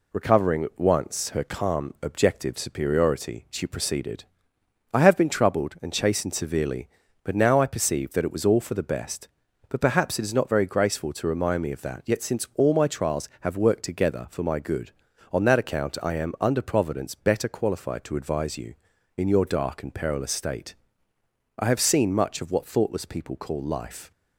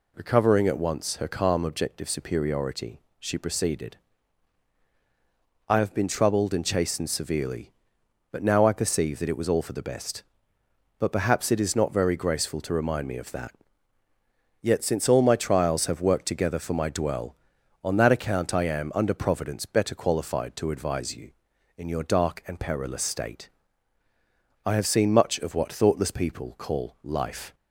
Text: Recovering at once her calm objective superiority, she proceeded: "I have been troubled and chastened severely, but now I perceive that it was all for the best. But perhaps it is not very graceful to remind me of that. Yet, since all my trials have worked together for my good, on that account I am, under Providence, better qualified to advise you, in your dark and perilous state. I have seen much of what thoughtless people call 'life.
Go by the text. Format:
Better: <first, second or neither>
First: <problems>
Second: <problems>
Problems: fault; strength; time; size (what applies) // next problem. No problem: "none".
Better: first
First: none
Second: says "dwell" for "good"; at 16.8 s